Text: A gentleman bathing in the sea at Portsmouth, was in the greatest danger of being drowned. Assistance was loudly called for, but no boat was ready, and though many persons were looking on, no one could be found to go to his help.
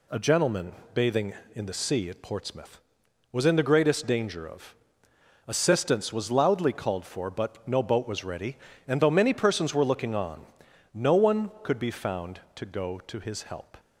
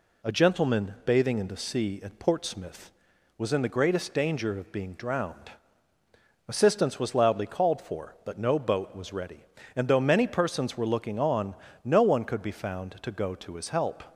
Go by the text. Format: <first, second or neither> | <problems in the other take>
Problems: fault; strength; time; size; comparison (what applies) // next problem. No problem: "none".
second | pauses between "gentleman" and "bathing"; slight; at 0.7 s; 0.22 s long // skips "being drowned"; at 5.1 s